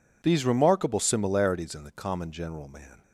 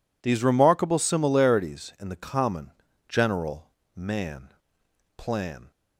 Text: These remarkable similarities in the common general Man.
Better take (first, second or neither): first